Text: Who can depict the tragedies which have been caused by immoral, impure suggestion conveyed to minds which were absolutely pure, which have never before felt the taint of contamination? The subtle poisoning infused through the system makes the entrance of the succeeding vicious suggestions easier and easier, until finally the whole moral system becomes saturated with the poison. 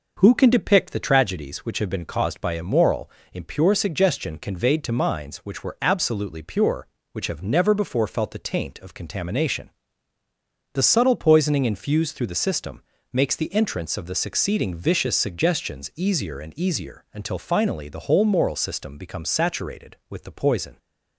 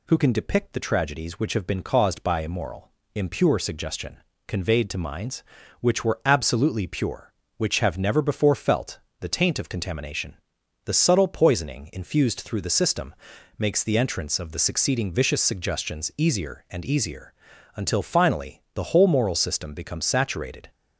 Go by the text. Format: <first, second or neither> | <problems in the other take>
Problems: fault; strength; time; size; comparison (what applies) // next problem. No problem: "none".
first | pauses between "suggestion" and "conveyed"; slight; at 4.1 s; 0.28 s long // pauses between "felt" and "the"; slight; at 9.0 s; 0.18 s long // pauses between "system" and "makes"; at 13.1 s; 0.44 s long; slight in the first // stops before "with the poison"; at 20.7 s